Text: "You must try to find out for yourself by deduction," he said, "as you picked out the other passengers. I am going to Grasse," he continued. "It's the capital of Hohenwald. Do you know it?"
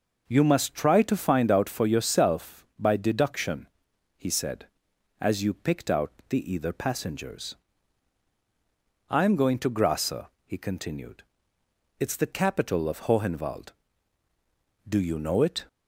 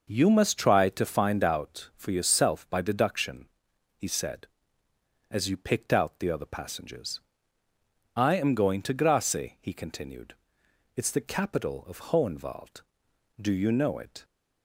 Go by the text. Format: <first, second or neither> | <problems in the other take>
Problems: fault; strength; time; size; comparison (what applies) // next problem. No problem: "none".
second | pauses between "out" and "the"; slight; at 6.1 s; 0.18 s long // says "either" for "other"; at 6.5 s